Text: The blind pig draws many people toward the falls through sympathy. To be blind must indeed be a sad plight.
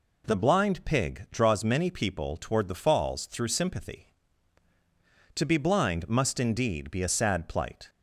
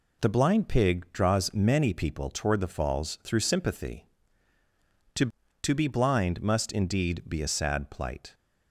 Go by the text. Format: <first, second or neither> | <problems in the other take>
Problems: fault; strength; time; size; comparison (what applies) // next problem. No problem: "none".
first | says "To" twice; at 5.6 s